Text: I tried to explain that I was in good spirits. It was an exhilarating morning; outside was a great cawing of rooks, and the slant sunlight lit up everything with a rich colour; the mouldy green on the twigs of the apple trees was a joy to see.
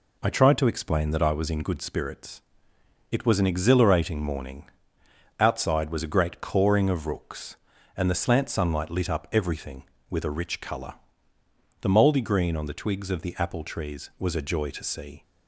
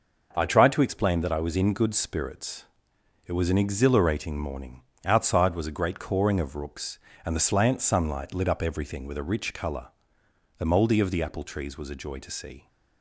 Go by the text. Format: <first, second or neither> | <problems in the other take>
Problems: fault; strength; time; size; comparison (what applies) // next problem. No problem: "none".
first | skips "green on the twigs"; at 11.0 s